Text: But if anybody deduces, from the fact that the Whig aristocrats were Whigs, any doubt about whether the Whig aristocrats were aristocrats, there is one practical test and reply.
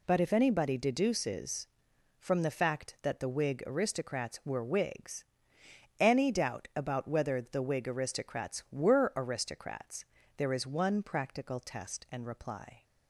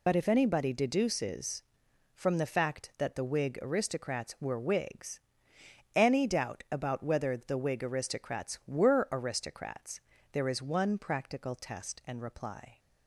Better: first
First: none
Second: loses the start of "But"; at 0.0 s; 60 ms

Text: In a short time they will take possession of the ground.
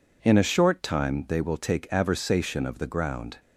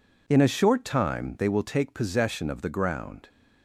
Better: second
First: says "aversation" for "possession"; at 1.8 s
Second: none

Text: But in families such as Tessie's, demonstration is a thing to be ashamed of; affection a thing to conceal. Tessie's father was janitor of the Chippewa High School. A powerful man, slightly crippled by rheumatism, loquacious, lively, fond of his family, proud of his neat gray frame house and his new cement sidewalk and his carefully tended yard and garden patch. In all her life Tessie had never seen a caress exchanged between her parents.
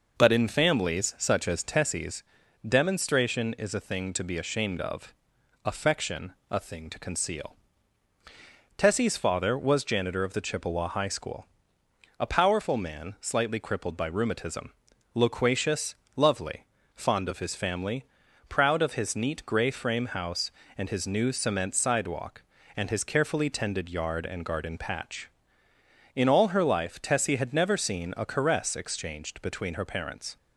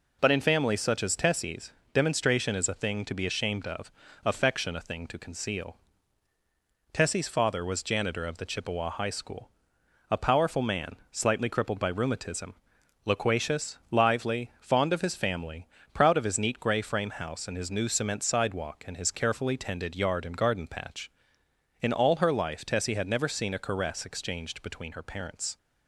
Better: second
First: pauses between "affection" and "a"; slight; at 6.3 s; 0.16 s long // says "lovely" for "lively"; at 16.1 s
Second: none

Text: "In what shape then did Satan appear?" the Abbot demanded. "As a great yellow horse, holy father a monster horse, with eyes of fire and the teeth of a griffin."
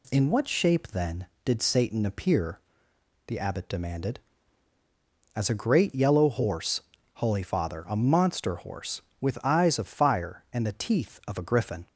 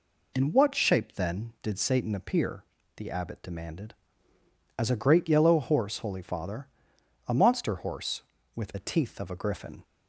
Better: first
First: none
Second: pauses between "father" and "a"; noticeable; at 6.6 s; 0.60 s long // skips "eyes of fire and"; at 8.7 s

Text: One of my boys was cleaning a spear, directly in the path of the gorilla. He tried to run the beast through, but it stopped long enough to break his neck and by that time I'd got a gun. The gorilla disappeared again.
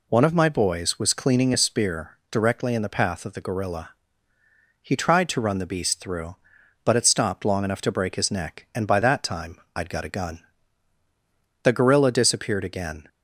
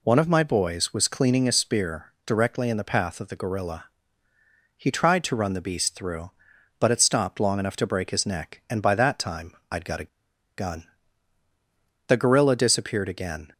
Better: first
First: pauses between "time" and "I'd"; slight; at 9.5 s; 0.18 s long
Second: pauses between "time" and "I'd"; slight; at 9.5 s; 0.18 s long // pauses between "a" and "gun"; noticeable; at 10.0 s; 0.49 s long

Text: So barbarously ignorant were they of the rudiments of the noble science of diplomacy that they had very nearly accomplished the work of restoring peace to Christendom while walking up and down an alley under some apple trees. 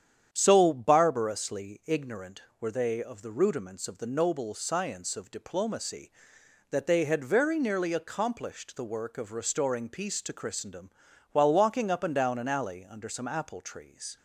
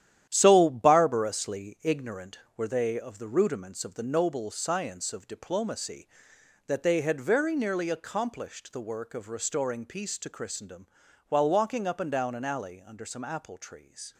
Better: first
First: starts louder than the rest; strong; until 1.3 s; 9 dB // pauses between "Christendom" and "while"; at 10.9 s; 0.42 s long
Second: gets quieter; strong; throughout; 8 dB // starts louder than the rest; strong; until 1.3 s; 11 dB // pauses between "Christendom" and "while"; at 10.8 s; 0.42 s long

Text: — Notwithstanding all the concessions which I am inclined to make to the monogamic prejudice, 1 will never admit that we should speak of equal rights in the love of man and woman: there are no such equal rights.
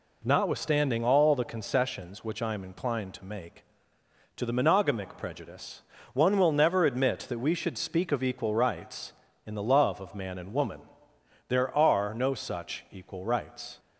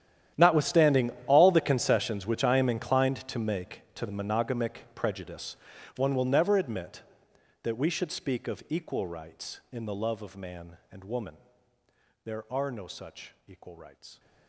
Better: first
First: none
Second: gets quieter; strong; throughout; 19.5 dB // pauses between "Notwithstanding" and "all"; slight; at 1.1 s; 0.16 s long

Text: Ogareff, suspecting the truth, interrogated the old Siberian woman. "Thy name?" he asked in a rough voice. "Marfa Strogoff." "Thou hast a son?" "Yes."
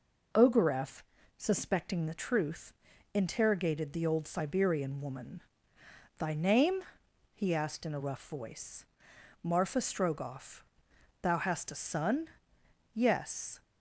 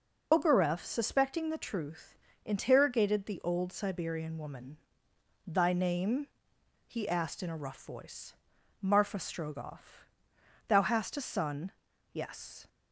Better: first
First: none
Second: loses the start of "Ogareff"; at 0.3 s; 70 ms

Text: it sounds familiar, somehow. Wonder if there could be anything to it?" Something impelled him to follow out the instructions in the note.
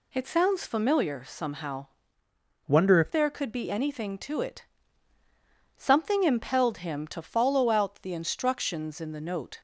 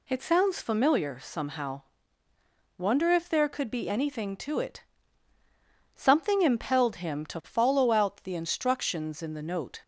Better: second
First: changes voice from "Wonder" to "if"; from 2.6 to 3.1 s; 0.5 s long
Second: none

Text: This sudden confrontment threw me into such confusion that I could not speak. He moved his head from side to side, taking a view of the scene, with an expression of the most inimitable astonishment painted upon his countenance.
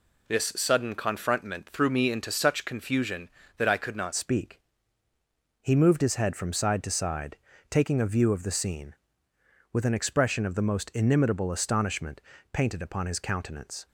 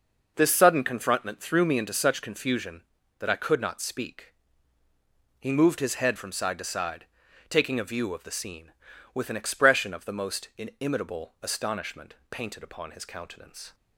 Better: second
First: changes voice at "speak"; from 4.1 s on; 9.7 s long // pauses between "astonishment" and "painted"; slight; at 12.2 s; 0.32 s long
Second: pauses between "astonishment" and "painted"; slight; at 12.1 s; 0.16 s long

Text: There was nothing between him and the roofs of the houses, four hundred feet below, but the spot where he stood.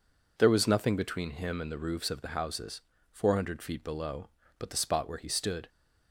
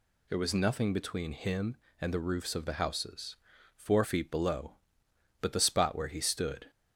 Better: first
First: none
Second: skips "hundred"; at 4.0 s

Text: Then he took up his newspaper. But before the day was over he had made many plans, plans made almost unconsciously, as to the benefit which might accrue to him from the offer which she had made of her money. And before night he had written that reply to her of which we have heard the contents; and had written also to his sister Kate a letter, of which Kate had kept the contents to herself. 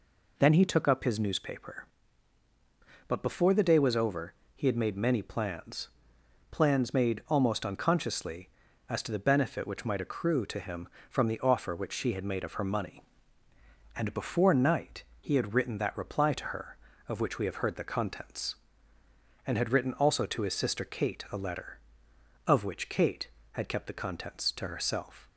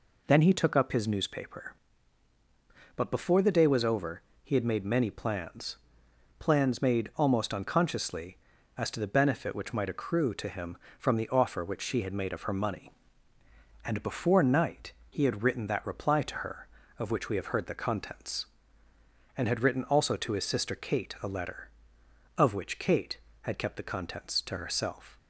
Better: neither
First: pauses between "over" and "he"; slight; at 4.3 s; 0.24 s long // pauses between "night" and "he"; slight; at 15.0 s; 0.16 s long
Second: pauses between "over" and "he"; slight; at 4.2 s; 0.24 s long // pauses between "night" and "he"; slight; at 14.9 s; 0.16 s long

